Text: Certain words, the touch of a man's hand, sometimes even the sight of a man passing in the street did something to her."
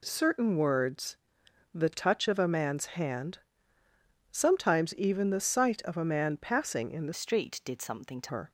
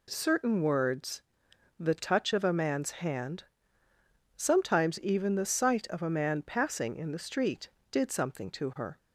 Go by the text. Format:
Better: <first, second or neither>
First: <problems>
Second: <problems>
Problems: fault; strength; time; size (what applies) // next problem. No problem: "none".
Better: second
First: changes voice from "street" to "to"; from 7.1 to 8.2 s; 1.1 s long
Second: none